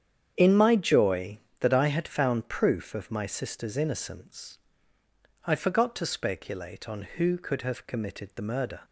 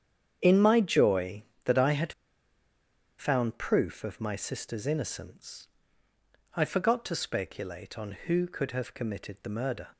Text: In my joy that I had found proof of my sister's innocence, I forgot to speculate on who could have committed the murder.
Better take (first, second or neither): first